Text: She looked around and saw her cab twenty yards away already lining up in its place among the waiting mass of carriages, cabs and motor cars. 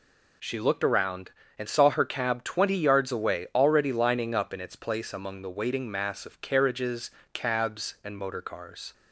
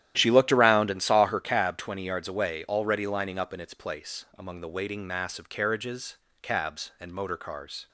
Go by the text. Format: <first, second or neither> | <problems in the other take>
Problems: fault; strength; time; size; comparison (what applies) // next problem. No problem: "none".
first | starts louder than the rest; strong; until 1.5 s; 12 dB